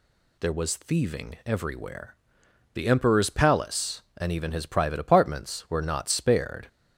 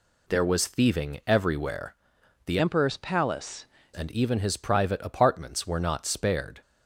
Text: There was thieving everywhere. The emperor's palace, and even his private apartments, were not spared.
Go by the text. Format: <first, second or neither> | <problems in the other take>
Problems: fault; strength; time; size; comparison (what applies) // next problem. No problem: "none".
first | changes voice from "emperor's" to "palace"; from 2.5 to 3.6 s; 1.1 s long